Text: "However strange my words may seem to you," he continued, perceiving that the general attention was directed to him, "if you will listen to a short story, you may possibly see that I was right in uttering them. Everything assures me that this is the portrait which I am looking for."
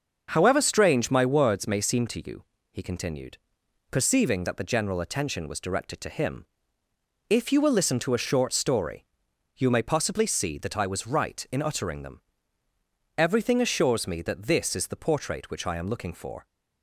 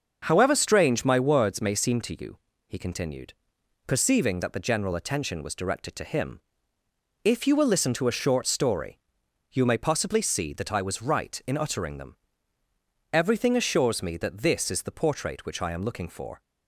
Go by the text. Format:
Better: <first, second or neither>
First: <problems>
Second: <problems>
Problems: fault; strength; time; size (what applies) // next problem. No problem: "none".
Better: neither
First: starts louder than the rest; until 1.3 s; 6.5 dB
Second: starts louder than the rest; until 1.2 s; 6.5 dB